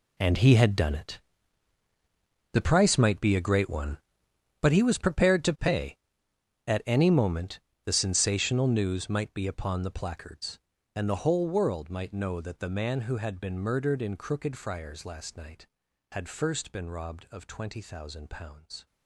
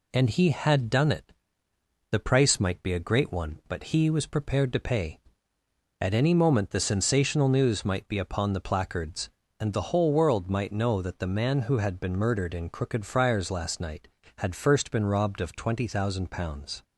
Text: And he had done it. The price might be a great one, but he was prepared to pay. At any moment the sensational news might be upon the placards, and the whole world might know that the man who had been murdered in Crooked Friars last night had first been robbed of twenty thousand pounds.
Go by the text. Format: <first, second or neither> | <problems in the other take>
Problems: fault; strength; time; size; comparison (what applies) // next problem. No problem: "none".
second | gets quieter; strong; throughout; 15 dB // pauses between "moment" and "the"; slight; at 7.5 s; 0.26 s long